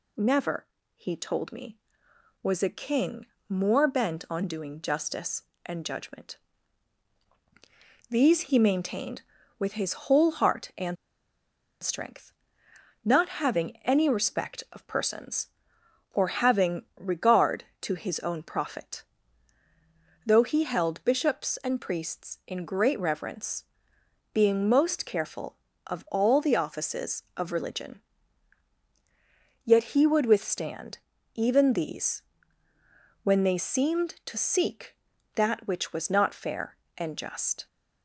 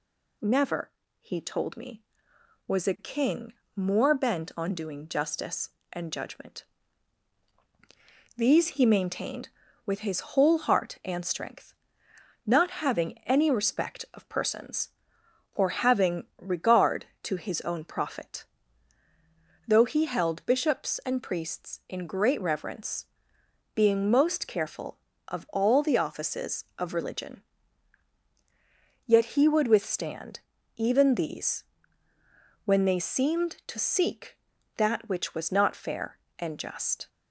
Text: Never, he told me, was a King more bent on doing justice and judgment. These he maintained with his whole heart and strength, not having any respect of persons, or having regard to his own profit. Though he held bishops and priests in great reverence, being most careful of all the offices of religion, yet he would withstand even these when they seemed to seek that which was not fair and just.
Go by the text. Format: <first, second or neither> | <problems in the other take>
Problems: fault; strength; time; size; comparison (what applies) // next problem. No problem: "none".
second | pauses between "King" and "more"; slight; at 3.2 s; 0.24 s long; slight in the second // pauses between "and" and "strength"; noticeable; at 10.9 s; 0.86 s long // pauses between "having" and "regard"; slight; at 16.8 s; 0.16 s long; slight in the second // pauses between "withstand" and "even"; slight; at 30.9 s; 0.36 s long; slight in the second // pauses between "these" and "when"; at 32.2 s; 1.0 s long; also in the second